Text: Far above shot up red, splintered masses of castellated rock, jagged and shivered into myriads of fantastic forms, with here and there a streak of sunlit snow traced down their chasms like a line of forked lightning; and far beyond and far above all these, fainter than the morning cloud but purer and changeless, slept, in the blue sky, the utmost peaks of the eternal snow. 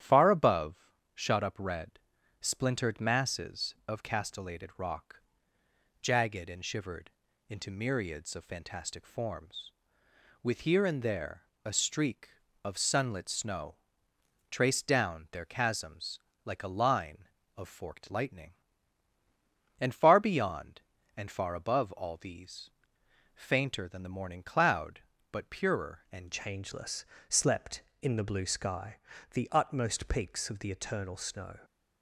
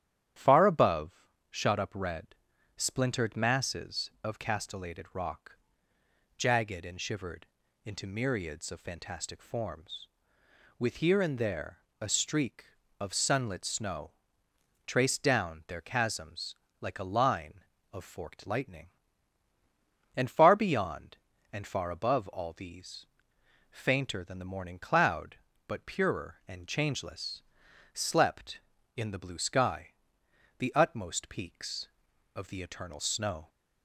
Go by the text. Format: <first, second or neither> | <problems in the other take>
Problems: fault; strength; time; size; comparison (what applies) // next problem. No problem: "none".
second | starts louder than the rest; strong; until 1.2 s; 10.5 dB; strong in the second // pauses between "above" and "shot"; slight; at 0.8 s; 0.24 s long; slight in the second // pauses between "shivered" and "into"; at 7.1 s; 0.38 s long; also in the second // pauses between "there" and "a"; slight; at 11.4 s; 0.20 s long; slight in the second // pauses between "snow" and "traced"; noticeable; at 13.7 s; 0.74 s long; noticeable in the second // pauses between "chasms" and "like"; slight; at 16.1 s; 0.28 s long; slight in the second // changes voice at "changeless"; from 26.3 s on; 5.2 s long